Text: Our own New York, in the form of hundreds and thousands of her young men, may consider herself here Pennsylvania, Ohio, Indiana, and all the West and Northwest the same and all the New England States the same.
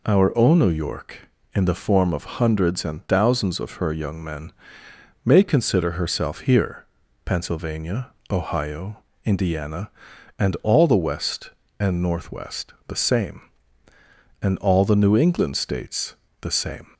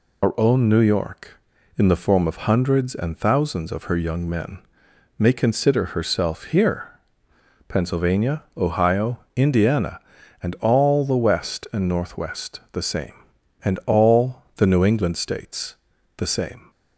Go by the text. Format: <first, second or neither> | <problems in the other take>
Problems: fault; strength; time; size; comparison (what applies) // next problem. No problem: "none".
first | loses the start of "Our"; at 0.2 s; 60 ms // pauses between "here" and "Pennsylvania"; noticeable; at 6.8 s; 0.78 s long; also in the first // pauses between "States" and "the"; at 15.7 s; 0.40 s long; slight in the first